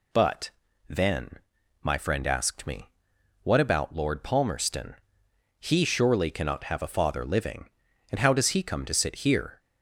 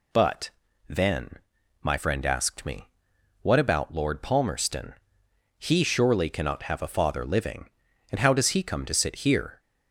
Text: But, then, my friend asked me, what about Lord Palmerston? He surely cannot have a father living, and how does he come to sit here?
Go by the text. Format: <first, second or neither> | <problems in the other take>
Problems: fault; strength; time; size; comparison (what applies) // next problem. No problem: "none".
neither | none